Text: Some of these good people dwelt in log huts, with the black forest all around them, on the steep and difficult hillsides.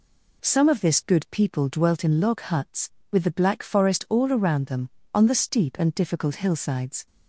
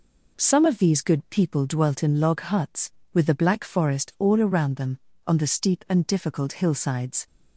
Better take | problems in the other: second | says "this" for "these"; at 0.8 s

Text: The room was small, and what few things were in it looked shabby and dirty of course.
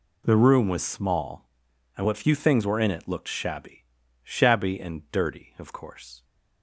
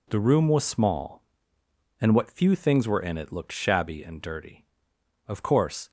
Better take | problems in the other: second | says "shabby" twice; at 4.2 s

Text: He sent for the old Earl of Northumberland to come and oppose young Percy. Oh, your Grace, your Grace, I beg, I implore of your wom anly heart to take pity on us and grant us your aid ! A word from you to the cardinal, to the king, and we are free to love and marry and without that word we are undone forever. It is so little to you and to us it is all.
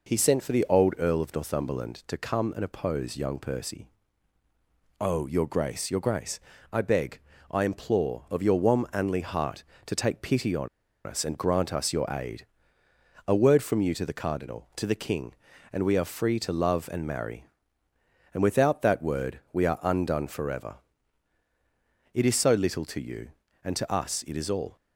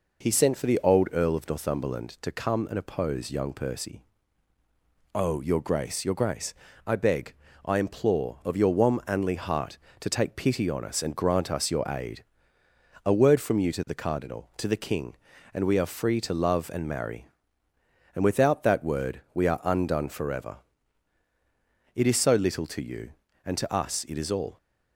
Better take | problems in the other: second | pauses between "on" and "us"; at 10.6 s; 0.39 s long

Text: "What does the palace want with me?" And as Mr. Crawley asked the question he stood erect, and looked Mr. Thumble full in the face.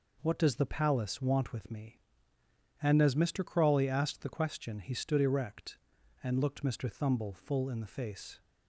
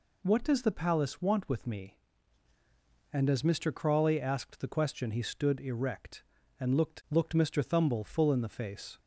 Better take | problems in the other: first | says "looked" twice; at 7.0 s

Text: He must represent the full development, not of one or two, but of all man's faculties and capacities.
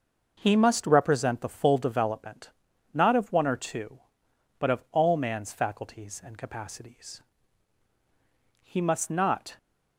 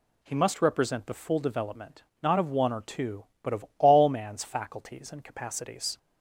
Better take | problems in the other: second | goes on to say "He must not"; noticeable; from 8.6 s on; 0.96 s long

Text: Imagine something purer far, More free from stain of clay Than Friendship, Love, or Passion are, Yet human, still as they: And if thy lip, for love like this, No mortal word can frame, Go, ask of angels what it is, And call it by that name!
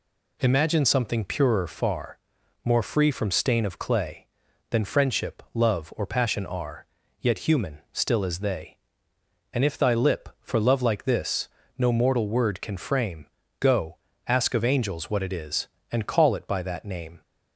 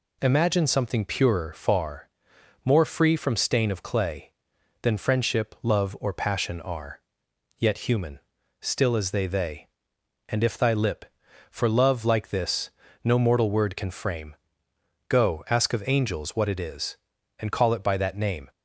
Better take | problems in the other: first | says "they" twice; at 9.2 s

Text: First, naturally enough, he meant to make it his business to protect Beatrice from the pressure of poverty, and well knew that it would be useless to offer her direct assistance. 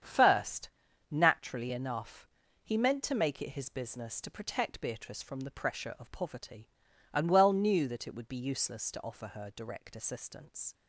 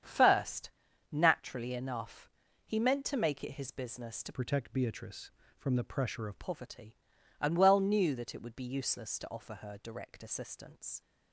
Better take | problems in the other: first | starts louder than the rest; strong; until 1.4 s; 8 dB; strong in the first // changes voice from "protect" to "of"; from 4.3 to 6.3 s; 2.0 s long

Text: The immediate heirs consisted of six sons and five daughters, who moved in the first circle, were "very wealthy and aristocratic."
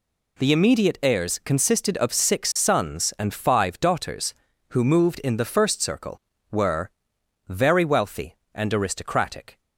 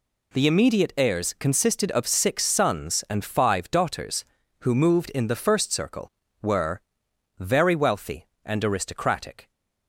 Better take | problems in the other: neither | pauses between "were" and "very"; noticeable; the same in both

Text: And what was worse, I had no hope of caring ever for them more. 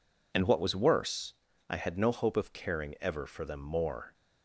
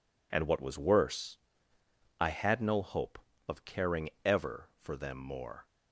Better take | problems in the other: neither | none

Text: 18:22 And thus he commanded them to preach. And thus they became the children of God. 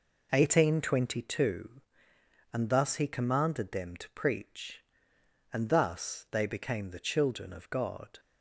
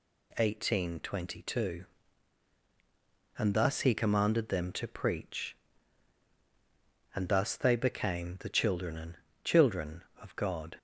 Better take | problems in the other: first | says "children" twice; at 9.4 s

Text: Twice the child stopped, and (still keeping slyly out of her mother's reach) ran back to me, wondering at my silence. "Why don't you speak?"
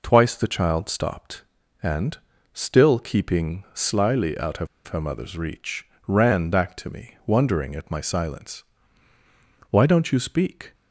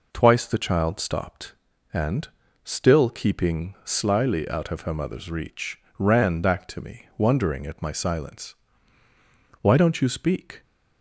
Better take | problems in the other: second | pauses between "of" and "her"; slight; at 4.6 s; 0.20 s long

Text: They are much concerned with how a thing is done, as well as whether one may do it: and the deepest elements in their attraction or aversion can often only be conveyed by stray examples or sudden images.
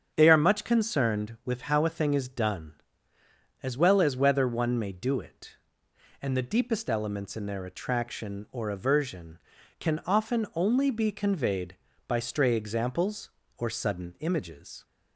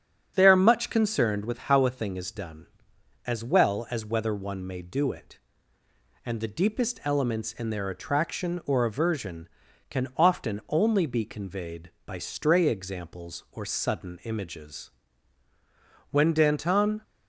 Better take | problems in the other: first | starts louder than the rest; strong; until 1.3 s; 7.5 dB; strong in the first // goes on to say "When Danton"; noticeable; from 16.1 s on; 0.92 s long

